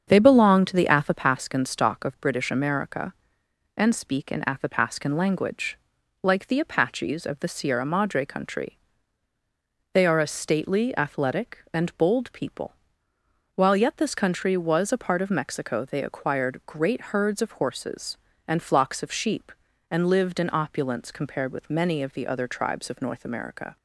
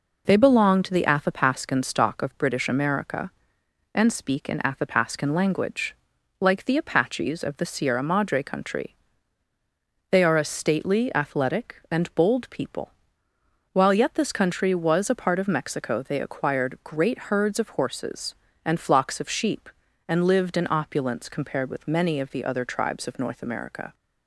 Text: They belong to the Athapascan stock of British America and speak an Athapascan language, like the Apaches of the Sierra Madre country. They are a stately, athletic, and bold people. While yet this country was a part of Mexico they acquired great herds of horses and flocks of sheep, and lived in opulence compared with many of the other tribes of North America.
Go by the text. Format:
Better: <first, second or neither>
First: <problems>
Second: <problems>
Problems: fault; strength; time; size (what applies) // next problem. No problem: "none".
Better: second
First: starts louder than the rest; strong; until 1.3 s; 7.5 dB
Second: none